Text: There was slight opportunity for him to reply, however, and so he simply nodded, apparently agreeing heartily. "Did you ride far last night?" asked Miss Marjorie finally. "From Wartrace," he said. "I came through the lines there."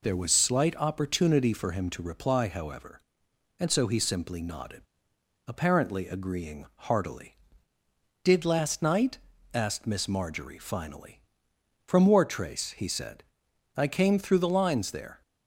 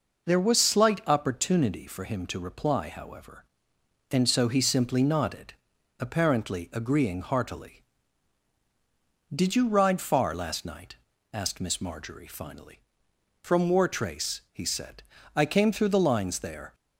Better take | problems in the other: second | skips "you ride far"; at 8.4 s

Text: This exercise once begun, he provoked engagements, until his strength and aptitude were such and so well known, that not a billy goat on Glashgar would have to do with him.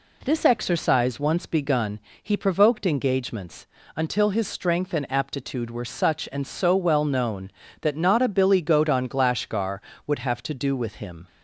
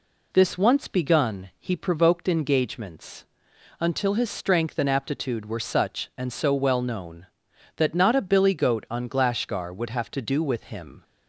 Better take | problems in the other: first | skips "exercise"; at 0.5 s

